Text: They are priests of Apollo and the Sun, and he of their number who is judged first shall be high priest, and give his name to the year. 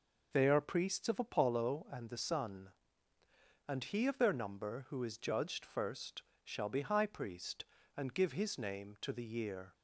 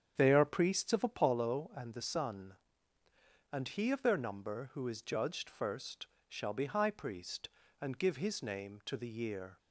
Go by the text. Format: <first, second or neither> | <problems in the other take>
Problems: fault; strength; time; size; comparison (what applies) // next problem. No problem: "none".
first | starts louder than the rest; strong; until 1.3 s; 8.5 dB // pauses between "first" and "shall"; slight; at 6.0 s; 0.22 s long; slight in the first